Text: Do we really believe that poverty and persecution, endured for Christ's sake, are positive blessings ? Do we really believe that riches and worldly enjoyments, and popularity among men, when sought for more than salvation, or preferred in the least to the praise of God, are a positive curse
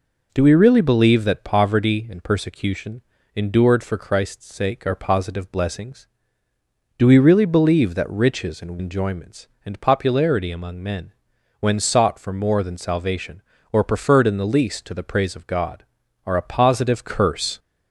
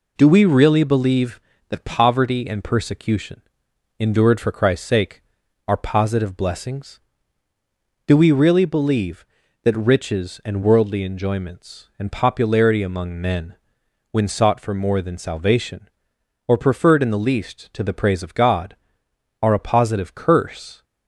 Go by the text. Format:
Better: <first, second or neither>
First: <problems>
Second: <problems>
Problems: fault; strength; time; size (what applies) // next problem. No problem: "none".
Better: second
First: skips "worldly"; at 8.7 s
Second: none